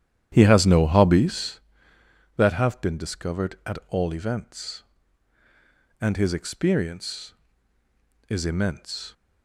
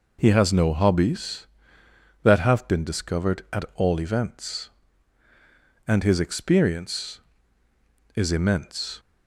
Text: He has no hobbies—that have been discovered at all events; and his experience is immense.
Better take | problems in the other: second | starts louder than the rest; strong; until 1.7 s; 11 dB

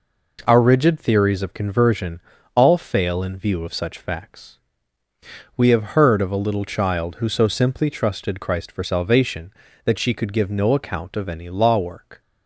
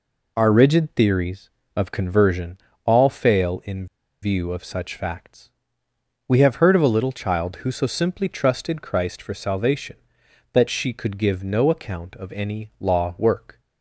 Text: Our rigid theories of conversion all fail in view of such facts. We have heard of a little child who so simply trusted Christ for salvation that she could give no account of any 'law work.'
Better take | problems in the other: first | pauses between "conversion" and "all"; slight; at 2.5 s; 0.28 s long; slight in the first // pauses between "in" and "view"; at 3.8 s; 0.37 s long

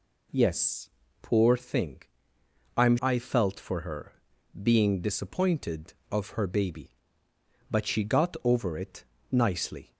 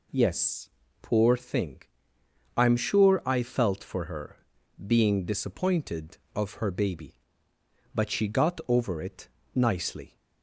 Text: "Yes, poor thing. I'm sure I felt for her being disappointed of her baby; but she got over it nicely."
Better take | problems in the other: second | skips "sure"; at 2.9 s // pauses between "her" and "being"; at 4.1 s; 0.42 s long; also in the second // pauses between "it" and "nicely"; slight; at 9.0 s; 0.26 s long; slight in the second

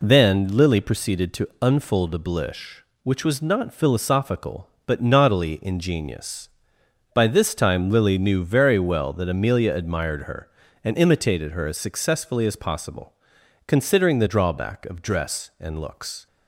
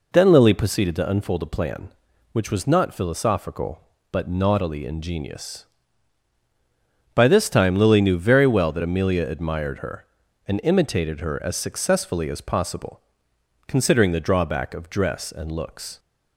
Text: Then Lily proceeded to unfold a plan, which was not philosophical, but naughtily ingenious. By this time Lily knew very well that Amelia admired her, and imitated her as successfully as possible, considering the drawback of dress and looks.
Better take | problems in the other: second | says "blish" for "plan"; at 2.1 s

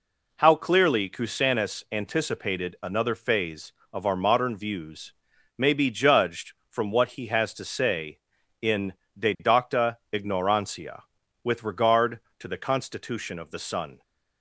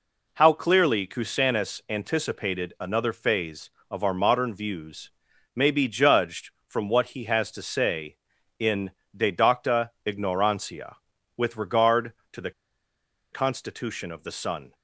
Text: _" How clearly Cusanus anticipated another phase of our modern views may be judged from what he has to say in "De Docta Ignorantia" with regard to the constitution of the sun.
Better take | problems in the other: first | pauses between "views" and "may"; noticeable; at 5.0 s; 0.46 s long; noticeable in the first // pauses between "in" and "De"; slight; at 8.9 s; 0.26 s long; slight in the first // pauses between "the" and "constitution"; noticeable; at 12.5 s; 0.82 s long

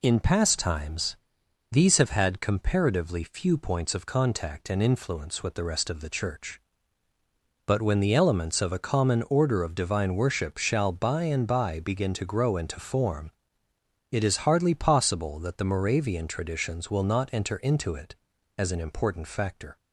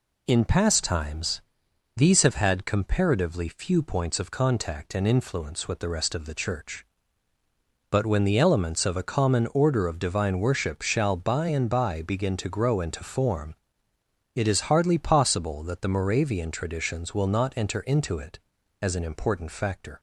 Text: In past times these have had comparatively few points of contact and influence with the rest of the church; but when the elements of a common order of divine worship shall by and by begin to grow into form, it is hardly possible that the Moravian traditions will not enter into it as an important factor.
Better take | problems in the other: neither | pauses between "times" and "these"; noticeable; the same in both

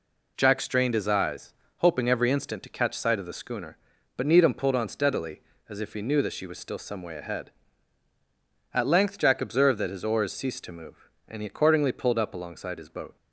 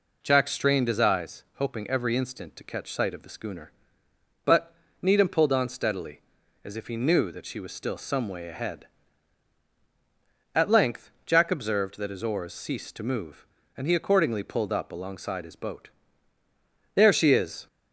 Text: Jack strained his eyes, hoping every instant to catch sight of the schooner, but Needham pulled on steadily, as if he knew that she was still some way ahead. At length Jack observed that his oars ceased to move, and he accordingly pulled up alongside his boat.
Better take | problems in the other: first | pauses between "but" and "Needham"; slight; at 4.7 s; 0.26 s long // goes on to say "There she is"; noticeable; from 16.9 s on; 0.72 s long

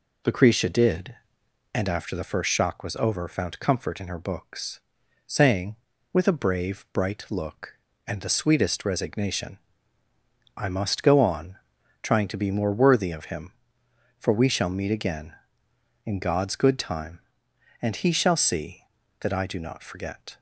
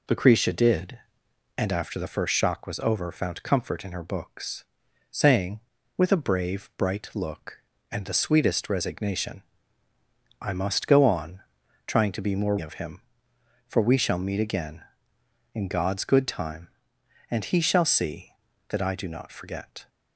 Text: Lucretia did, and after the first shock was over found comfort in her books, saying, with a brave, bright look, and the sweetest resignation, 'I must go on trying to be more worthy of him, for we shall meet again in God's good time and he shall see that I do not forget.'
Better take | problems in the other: first | pauses between "on" and "trying"; noticeable; at 11.3 s; 0.46 s long; noticeable in the first // skips "worthy"; at 12.5 s

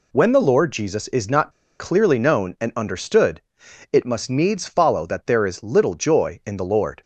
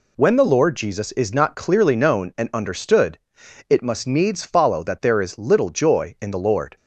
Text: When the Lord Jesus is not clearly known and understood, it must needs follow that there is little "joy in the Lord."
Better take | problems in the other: second | pauses between "not" and "clearly"; slight; at 1.5 s; 0.27 s long

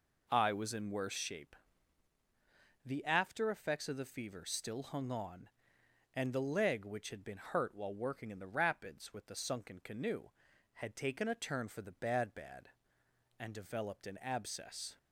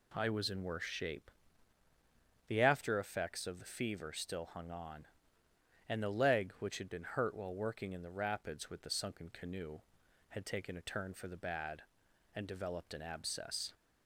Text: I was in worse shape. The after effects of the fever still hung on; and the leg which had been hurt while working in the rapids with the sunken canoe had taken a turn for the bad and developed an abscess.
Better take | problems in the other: second | says "bad" twice; at 12.3 s

